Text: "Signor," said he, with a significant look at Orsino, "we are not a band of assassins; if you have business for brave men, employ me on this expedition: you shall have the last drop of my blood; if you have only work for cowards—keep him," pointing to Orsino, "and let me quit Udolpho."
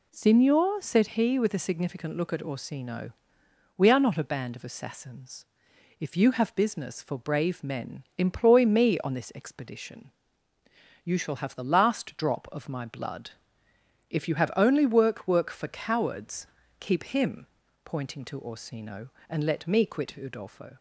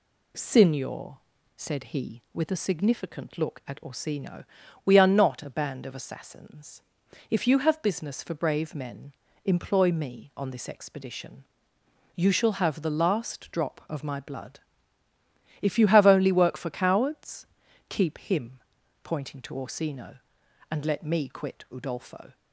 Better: second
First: says "work" twice; at 15.2 s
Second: none

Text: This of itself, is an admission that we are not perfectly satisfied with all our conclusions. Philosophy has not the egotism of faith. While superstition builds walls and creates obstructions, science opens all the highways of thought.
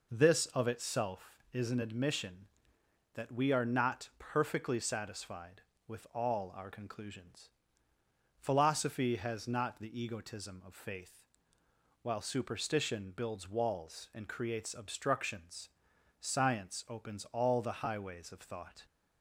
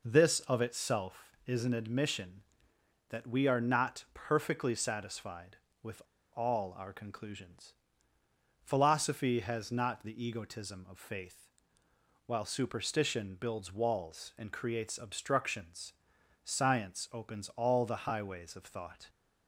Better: first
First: none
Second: pauses between "with" and "all"; slight; at 6.0 s; 0.32 s long

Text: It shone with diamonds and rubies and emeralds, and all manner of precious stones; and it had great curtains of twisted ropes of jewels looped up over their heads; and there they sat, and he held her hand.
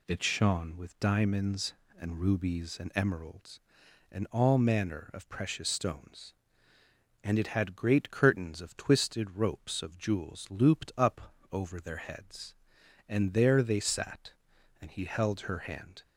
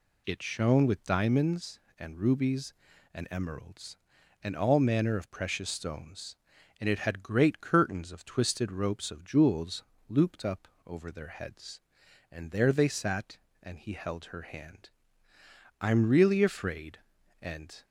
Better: first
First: pauses between "up" and "over"; slight; at 11.3 s; 0.18 s long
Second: pauses between "jewels" and "looped"; slight; at 9.8 s; 0.24 s long // pauses between "up" and "over"; slight; at 10.6 s; 0.20 s long // goes on to say "I'm really afraid and"; strong; from 15.8 s on; 2.0 s long

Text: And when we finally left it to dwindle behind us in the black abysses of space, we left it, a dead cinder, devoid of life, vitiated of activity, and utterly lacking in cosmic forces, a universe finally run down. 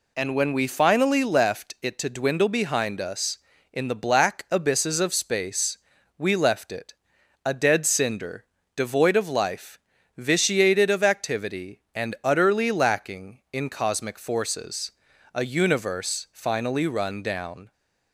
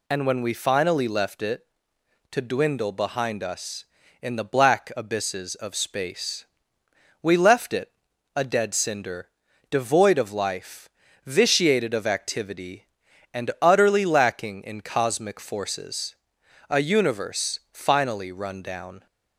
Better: neither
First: none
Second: none

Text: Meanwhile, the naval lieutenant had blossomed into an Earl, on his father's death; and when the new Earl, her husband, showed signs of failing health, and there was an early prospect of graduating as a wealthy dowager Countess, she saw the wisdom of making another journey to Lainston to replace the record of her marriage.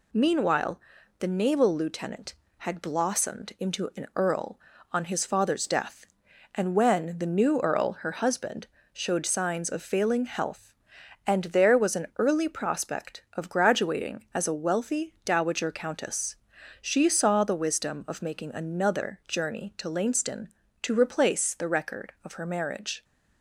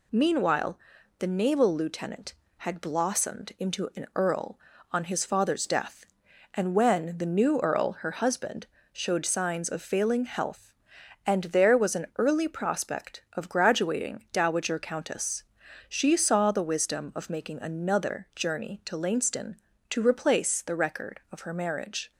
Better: first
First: none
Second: skips "as a wealthy"; at 14.2 s

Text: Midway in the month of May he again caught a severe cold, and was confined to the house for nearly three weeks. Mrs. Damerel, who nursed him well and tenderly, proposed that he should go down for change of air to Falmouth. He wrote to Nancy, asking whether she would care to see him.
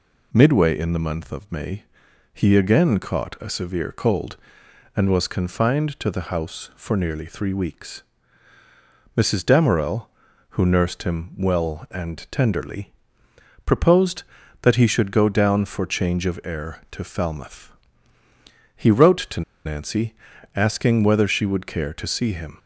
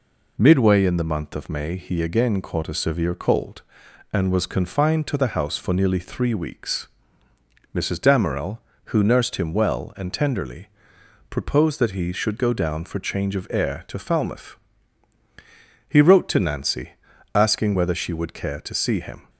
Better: second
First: pauses between "May" and "he"; noticeable; at 1.8 s; 0.50 s long // pauses between "to" and "Nancy"; slight; at 19.4 s; 0.24 s long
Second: none

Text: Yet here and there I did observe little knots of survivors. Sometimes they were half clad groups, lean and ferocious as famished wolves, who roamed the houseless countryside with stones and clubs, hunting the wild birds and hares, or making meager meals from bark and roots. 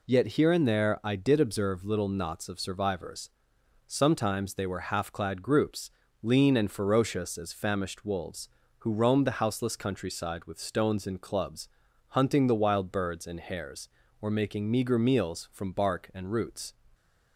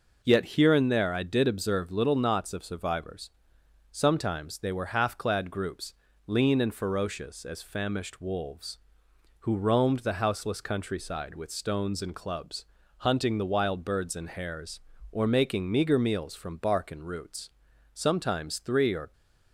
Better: first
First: none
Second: goes on to say "Sometimes three or"; noticeable; from 17.9 s on; 1.2 s long

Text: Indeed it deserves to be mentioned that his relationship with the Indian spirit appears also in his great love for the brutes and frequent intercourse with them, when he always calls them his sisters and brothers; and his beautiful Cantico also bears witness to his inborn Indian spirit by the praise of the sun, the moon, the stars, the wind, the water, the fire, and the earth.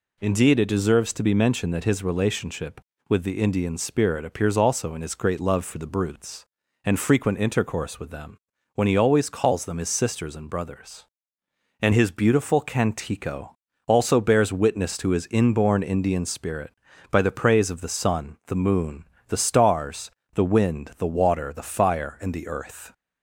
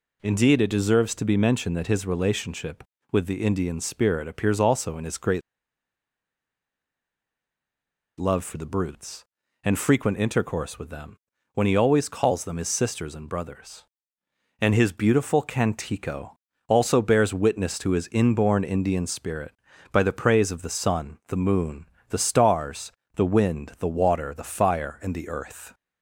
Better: first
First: pauses between "Cantico" and "also"; slight; at 13.5 s; 0.30 s long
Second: pauses between "great" and "love"; strong; at 5.4 s; 2.7 s long // pauses between "Cantico" and "also"; slight; at 16.3 s; 0.30 s long

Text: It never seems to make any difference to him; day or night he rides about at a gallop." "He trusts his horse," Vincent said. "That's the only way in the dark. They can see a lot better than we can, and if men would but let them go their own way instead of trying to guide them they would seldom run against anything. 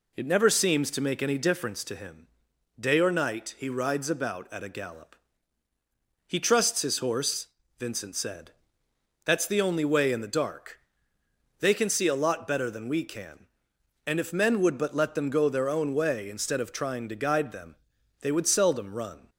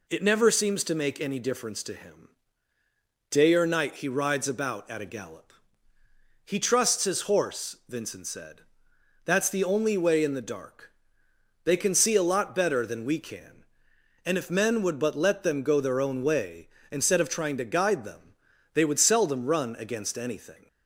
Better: second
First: pauses between "them" and "they"; noticeable; at 17.7 s; 0.46 s long // stops before "against anything"; at 19.2 s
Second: pauses between "them" and "they"; at 18.3 s; 0.38 s long

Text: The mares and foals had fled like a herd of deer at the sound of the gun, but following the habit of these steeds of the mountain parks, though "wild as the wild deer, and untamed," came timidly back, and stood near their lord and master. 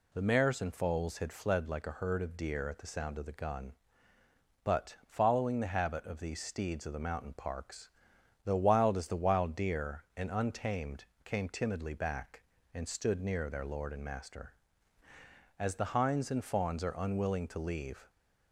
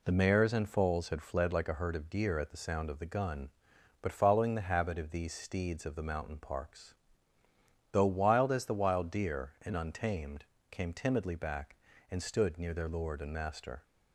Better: second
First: goes on to say "As the hinds and fawns are unwilling to leave"; strong; from 15.5 s on; 2.5 s long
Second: none

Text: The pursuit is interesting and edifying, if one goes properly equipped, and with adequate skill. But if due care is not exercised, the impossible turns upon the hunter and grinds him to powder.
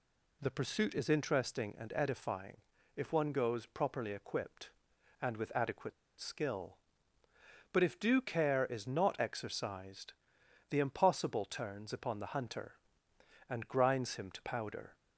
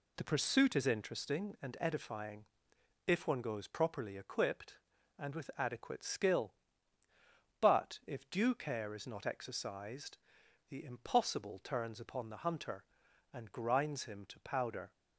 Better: second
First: pauses between "adequate" and "skill"; slight; at 5.9 s; 0.26 s long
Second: none

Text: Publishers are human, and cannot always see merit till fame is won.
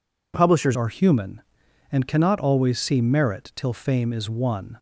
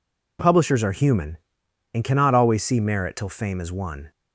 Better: second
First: changes voice at "are"; from 0.7 s on; 4.0 s long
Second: none

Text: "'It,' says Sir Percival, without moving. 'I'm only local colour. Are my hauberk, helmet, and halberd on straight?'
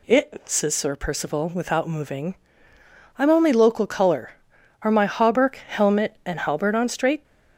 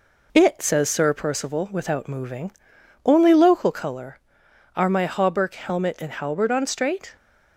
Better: first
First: none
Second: skips "I'm"; at 2.7 s

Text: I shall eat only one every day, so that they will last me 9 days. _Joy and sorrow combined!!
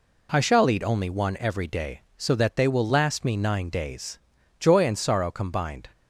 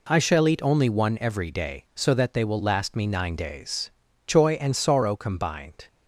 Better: neither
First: none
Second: none

